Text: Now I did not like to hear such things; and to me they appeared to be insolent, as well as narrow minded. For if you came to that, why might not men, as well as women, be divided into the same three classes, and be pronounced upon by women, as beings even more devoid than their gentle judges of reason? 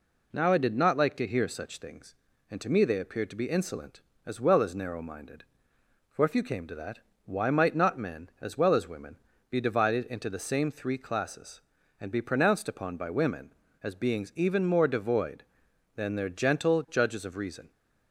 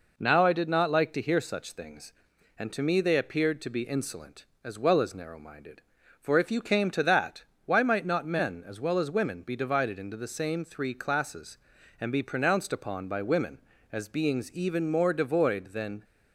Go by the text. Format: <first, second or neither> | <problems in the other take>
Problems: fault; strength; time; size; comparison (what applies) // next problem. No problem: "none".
first | stops before "their gentle judges of reason"; at 16.0 s